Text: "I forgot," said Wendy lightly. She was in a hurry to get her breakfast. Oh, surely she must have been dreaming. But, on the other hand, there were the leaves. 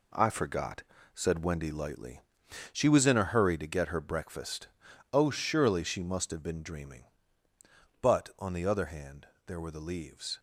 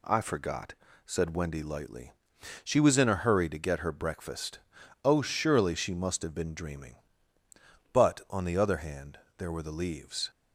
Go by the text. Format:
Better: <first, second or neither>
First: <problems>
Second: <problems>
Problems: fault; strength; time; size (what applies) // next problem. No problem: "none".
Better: second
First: gets quieter; strong; throughout; 8 dB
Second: none